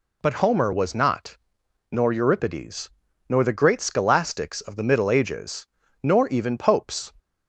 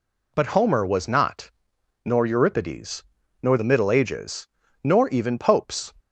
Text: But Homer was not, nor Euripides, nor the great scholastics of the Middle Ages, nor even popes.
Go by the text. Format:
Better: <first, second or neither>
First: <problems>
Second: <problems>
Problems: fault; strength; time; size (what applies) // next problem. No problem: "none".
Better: first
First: none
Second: skips "the great scholastics of"; at 3.5 s